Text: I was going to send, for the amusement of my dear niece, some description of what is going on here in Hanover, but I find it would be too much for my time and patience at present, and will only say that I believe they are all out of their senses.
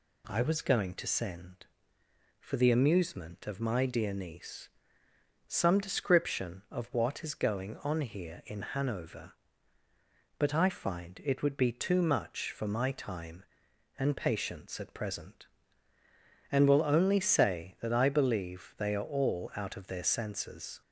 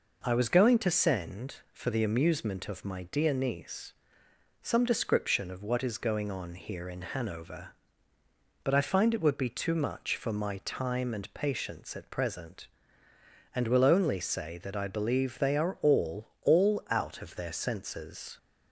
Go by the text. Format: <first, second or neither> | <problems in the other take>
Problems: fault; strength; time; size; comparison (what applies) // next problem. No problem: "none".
first | says "all" twice; at 16.4 s